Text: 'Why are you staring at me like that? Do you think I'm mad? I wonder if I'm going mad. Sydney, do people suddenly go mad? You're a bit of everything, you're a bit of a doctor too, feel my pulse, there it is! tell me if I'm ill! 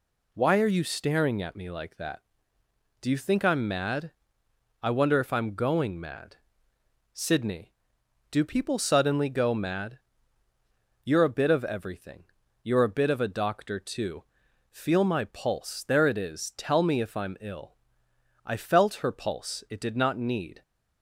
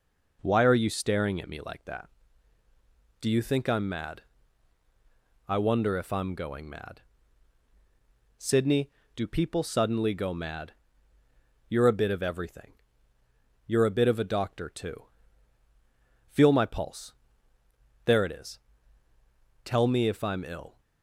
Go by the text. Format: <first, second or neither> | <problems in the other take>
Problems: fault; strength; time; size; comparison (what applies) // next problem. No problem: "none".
second | goes on to say "I felt her pulse it did not need"; strong; from 18.4 s on; 2.1 s long